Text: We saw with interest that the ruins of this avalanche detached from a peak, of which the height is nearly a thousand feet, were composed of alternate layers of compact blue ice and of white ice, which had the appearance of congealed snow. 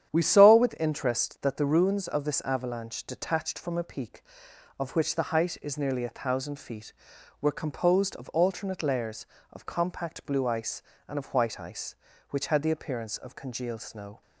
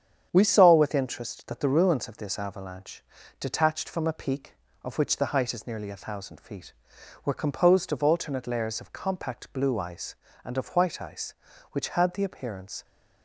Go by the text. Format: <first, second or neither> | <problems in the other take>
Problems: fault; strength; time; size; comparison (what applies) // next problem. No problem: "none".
first | starts louder than the rest; strong; until 1.3 s; 8.5 dB; strong in the first // pauses between "avalanche" and "detached"; at 3.0 s; 0.38 s long // stops before "of congealed snow"; at 12.8 s